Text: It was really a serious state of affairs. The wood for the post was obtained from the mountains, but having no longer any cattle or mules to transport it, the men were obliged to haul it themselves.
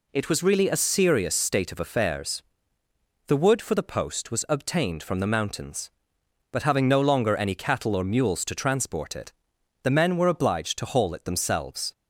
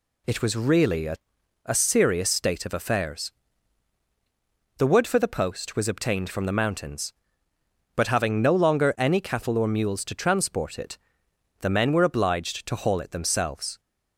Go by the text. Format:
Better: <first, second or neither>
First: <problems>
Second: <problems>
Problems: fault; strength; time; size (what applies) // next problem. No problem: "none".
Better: first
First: none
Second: says "a" twice; at 1.6 s